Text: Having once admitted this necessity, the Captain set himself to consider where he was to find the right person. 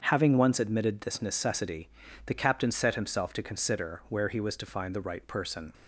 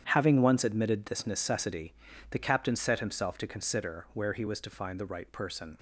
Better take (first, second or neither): first